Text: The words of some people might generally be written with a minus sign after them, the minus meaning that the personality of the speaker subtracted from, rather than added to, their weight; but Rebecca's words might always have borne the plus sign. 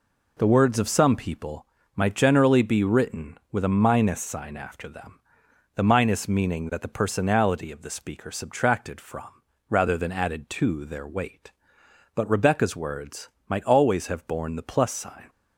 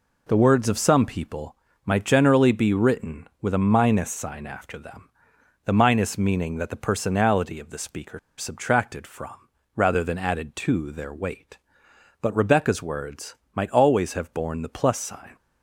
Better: first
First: pauses between "people" and "might"; slight; at 1.6 s; 0.30 s long // pauses between "words" and "might"; slight; at 13.2 s; 0.22 s long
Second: pauses between "people" and "might"; slight; at 1.5 s; 0.30 s long // pauses between "speaker" and "subtracted"; slight; at 8.1 s; 0.18 s long // pauses between "words" and "might"; slight; at 13.3 s; 0.22 s long

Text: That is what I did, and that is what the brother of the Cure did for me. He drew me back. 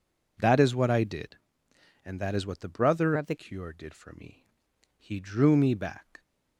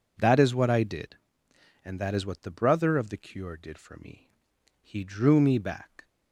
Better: second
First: changes voice from "of" to "the"; from 3.1 to 3.3 s; 0.2 s long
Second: none

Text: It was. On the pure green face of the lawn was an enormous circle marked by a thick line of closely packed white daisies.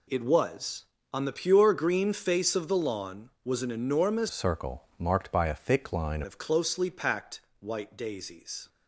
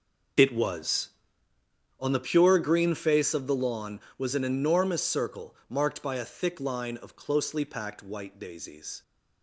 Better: second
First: changes voice from "circle" to "line"; from 4.2 to 6.2 s; 2.0 s long // pauses between "circle" and "marked"; slight; at 4.8 s; 0.16 s long // pauses between "packed" and "white"; slight; at 7.4 s; 0.18 s long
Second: none

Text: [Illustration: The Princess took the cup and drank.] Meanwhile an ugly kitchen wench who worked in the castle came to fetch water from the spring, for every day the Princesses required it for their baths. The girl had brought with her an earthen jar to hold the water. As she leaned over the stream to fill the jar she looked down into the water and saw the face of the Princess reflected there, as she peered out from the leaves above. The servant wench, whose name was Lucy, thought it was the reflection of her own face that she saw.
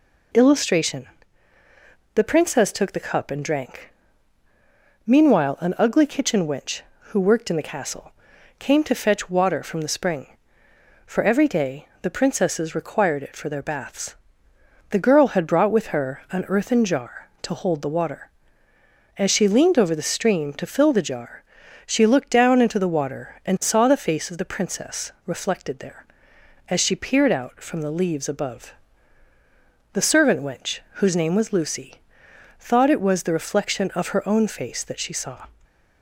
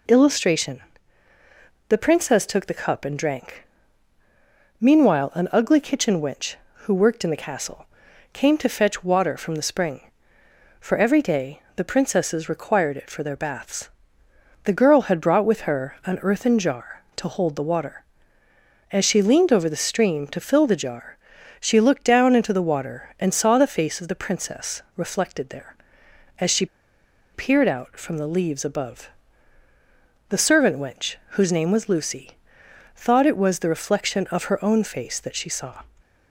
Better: first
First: pauses between "castle" and "came"; noticeable; at 8.1 s; 0.46 s long // pauses between "day" and "the"; slight; at 11.8 s; 0.16 s long // pauses between "jar" and "she"; at 21.4 s; 0.42 s long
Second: pauses between "castle" and "came"; noticeable; at 7.8 s; 0.46 s long // pauses between "day" and "the"; slight; at 11.5 s; 0.16 s long // pauses between "jar" and "she"; at 21.1 s; 0.42 s long // pauses between "she" and "peered"; noticeable; at 26.6 s; 0.68 s long

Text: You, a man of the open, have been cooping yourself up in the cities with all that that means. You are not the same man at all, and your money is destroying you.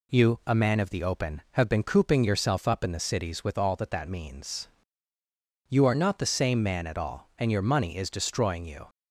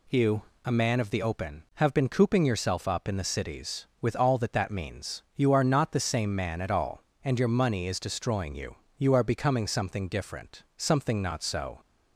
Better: first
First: none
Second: goes on to say "You are becoming something different something not so"; strong; from 8.9 s on; 2.8 s long

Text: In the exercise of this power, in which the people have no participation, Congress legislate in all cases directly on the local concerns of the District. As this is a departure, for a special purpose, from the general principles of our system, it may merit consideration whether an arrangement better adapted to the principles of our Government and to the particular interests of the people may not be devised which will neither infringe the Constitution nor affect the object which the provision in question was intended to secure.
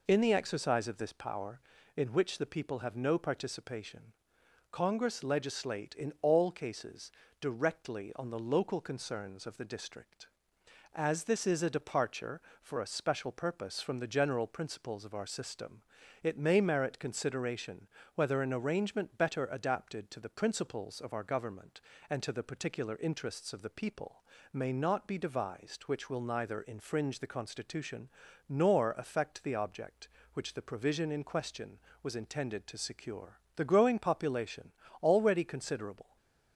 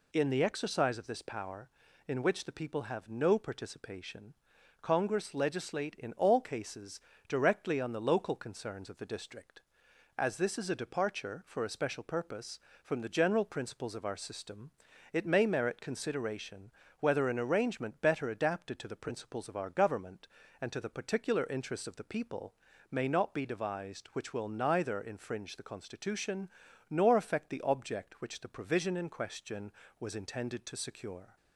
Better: second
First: pauses between "cases" and "directly"; slight; at 7.1 s; 0.30 s long // pauses between "consideration" and "whether"; slight; at 17.8 s; 0.26 s long // pauses between "people" and "may"; slight; at 24.2 s; 0.30 s long // pauses between "Constitution" and "nor"; at 28.0 s; 0.40 s long // goes on to say "The growing population already considerable"; strong; from 33.5 s on; 2.6 s long // stays silent after the last word; slight; from 36.0 s on; 0.5 s long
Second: pauses between "cases" and "directly"; slight; at 6.9 s; 0.28 s long // pauses between "consideration" and "whether"; slight; at 16.7 s; 0.28 s long // pauses between "people" and "may"; at 22.5 s; 0.38 s long // pauses between "Constitution" and "nor"; at 26.4 s; 0.42 s long

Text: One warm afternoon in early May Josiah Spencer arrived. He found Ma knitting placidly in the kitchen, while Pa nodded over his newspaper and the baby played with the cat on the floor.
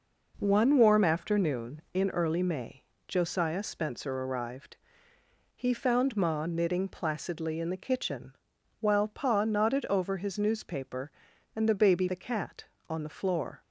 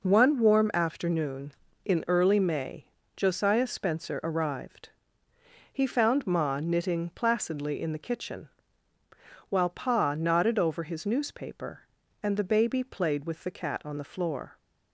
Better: second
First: pauses between "May" and "Josiah"; slight; at 2.8 s; 0.24 s long // skips "played with"; at 12.0 s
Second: pauses between "May" and "Josiah"; slight; at 2.8 s; 0.30 s long

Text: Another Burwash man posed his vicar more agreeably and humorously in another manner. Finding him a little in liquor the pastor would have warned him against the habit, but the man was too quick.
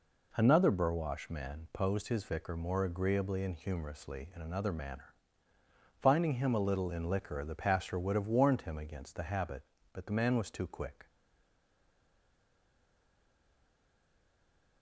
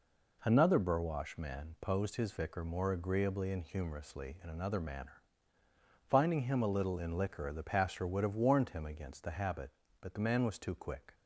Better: second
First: stays silent after the last word; strong; from 11.0 s on; 3.8 s long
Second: none

